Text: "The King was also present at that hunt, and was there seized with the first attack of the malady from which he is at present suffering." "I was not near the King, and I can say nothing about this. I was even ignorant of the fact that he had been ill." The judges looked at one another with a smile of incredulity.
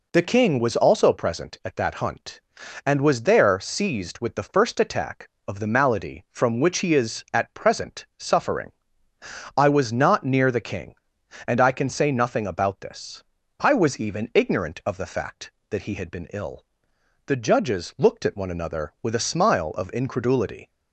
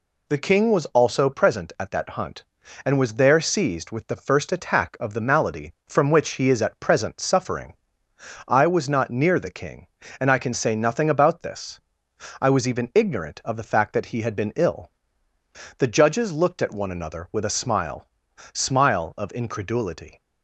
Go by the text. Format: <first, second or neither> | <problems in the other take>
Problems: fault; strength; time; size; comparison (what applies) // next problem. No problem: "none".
first | says "smile" twice; at 18.5 s